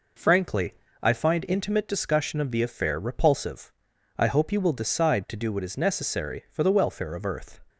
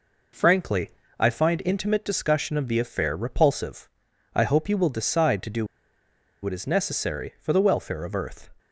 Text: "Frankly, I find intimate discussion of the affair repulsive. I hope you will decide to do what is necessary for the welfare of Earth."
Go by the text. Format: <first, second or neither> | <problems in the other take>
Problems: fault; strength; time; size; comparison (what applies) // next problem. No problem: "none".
first | pauses between "do" and "what"; noticeable; at 5.6 s; 0.78 s long